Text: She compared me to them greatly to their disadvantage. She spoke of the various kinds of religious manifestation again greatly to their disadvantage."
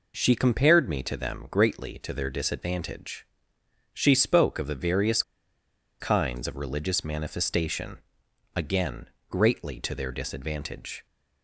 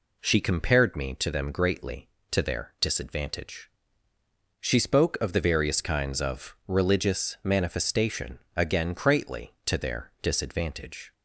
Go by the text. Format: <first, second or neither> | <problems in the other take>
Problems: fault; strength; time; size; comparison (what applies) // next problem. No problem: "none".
second | pauses between "various" and "kinds"; noticeable; at 5.2 s; 0.79 s long // pauses between "manifestation" and "again"; noticeable; at 7.9 s; 0.58 s long; slight in the second // pauses between "again" and "greatly"; slight; at 9.0 s; 0.22 s long